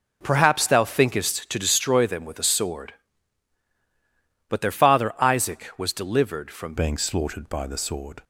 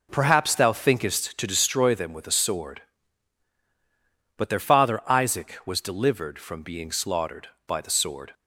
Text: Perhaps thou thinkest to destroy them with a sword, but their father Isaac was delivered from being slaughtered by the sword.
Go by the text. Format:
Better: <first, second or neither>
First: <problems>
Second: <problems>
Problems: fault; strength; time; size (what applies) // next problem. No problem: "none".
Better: second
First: changes voice at "being"; from 6.7 s on; 1.5 s long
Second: none